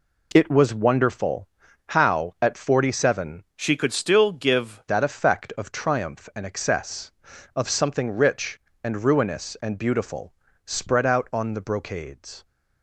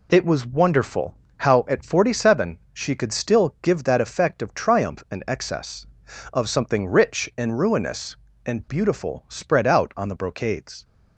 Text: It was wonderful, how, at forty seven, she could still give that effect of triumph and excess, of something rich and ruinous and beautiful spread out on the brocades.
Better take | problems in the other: second | changes voice from "she" to "give"; from 3.5 to 4.8 s; 1.3 s long // pauses between "beautiful" and "spread"; slight; at 10.3 s; 0.32 s long

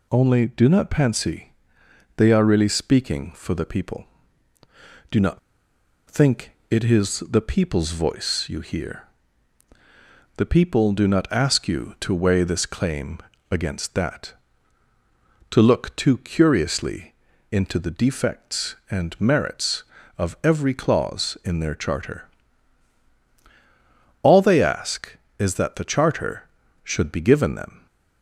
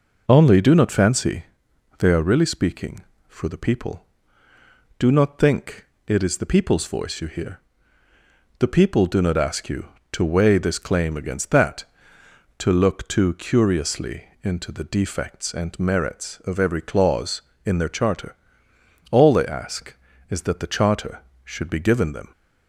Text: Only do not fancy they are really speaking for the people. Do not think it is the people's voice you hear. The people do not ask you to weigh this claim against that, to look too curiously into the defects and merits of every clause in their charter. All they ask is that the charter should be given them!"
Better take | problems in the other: second | pauses between "fancy" and "they"; noticeable; at 1.5 s; 0.64 s long; noticeable in the second // pauses between "not" and "think"; noticeable; at 5.3 s; 0.70 s long // pauses between "think" and "it"; slight; at 6.5 s; 0.18 s long; slight in the second // pauses between "claim" and "against"; slight; at 13.1 s; 0.32 s long // pauses between "curiously" and "into"; slight; at 17.1 s; 0.36 s long; slight in the second

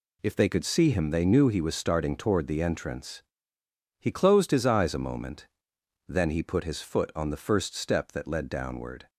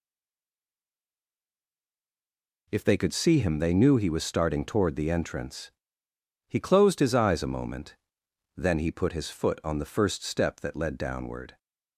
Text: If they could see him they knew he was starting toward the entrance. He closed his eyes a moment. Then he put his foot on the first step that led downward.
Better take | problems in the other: first | stays silent before the first word; strong; until 2.6 s; 2.6 s long

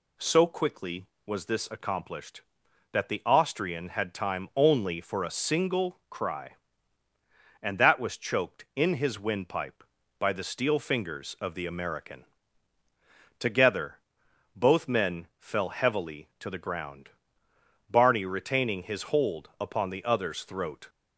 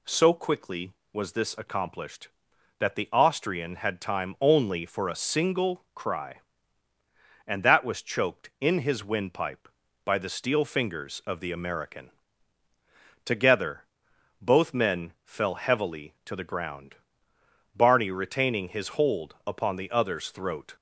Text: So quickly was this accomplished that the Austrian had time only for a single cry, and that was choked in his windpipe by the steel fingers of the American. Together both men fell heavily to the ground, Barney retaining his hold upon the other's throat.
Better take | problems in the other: neither | pauses between "Together" and "both"; noticeable; the same in both

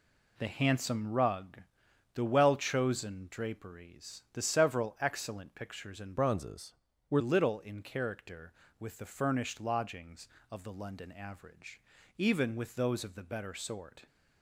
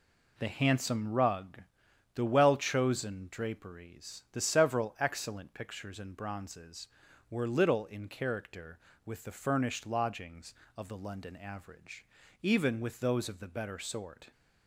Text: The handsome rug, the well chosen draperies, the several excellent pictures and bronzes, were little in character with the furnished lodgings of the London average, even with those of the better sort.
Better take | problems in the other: second | changes voice from "bronzes" to "were"; from 6.1 to 7.2 s; 1.1 s long

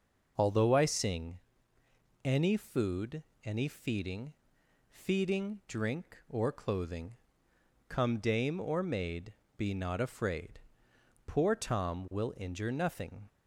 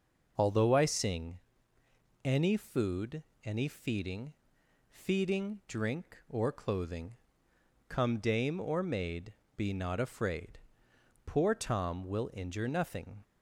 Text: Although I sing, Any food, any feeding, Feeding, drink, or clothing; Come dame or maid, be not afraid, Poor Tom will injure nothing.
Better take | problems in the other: neither | none

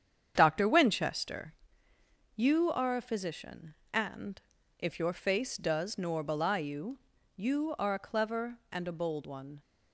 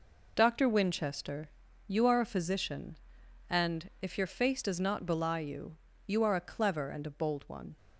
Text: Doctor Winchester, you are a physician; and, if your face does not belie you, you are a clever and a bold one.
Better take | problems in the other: second | starts louder than the rest; strong; until 1.3 s; 8.5 dB // says "nor" for "not"; at 5.9 s

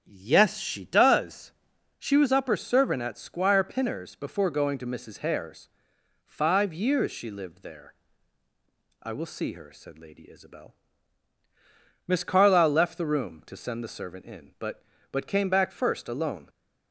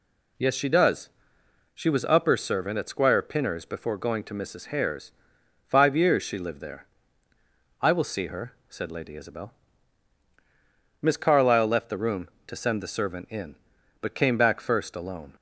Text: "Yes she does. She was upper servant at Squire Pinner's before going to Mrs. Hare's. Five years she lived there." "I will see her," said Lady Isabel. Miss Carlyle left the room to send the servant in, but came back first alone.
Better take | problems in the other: second | starts louder than the rest; strong; until 1.0 s; 7 dB // says "but" twice; at 15.1 s

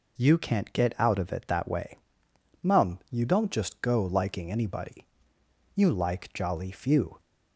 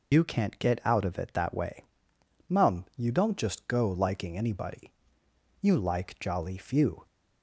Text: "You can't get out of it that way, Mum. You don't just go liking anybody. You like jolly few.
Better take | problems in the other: first | loses the start of "You"; at 0.1 s; 85 ms

